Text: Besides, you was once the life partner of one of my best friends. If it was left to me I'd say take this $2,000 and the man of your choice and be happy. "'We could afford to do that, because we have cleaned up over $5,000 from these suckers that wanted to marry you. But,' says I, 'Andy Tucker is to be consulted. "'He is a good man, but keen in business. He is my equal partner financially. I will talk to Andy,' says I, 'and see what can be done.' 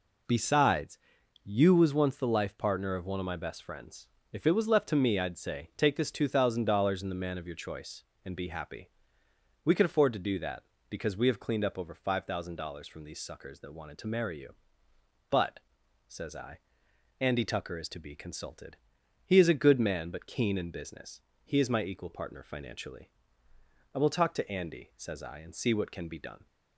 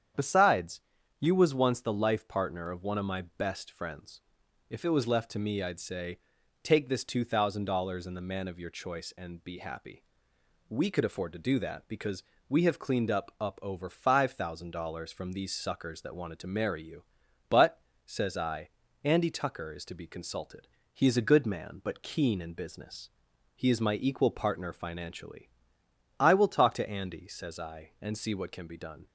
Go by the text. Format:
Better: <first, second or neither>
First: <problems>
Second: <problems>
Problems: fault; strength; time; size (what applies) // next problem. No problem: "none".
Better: first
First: none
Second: starts louder than the rest; strong; until 1.5 s; 8.5 dB // pauses between "say" and "take"; noticeable; at 6.1 s; 0.46 s long // pauses between "because" and "we"; slight; at 12.2 s; 0.24 s long // says "up" twice; at 13.3 s